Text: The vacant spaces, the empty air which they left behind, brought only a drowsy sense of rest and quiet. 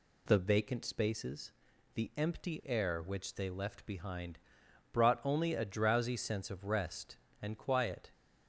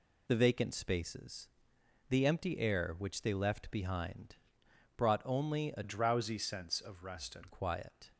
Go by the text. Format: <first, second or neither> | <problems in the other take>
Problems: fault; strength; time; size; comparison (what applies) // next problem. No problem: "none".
first | changes voice from "drowsy" to "and"; from 5.8 to 7.4 s; 1.6 s long